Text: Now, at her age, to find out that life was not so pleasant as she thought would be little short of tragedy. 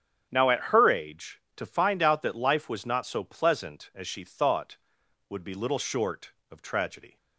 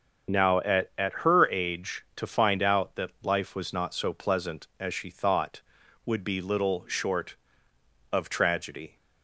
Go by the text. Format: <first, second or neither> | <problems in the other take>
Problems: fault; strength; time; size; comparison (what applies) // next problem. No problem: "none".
first | starts louder than the rest; until 1.5 s; 7 dB; strong in the first // says "at" twice; at 0.9 s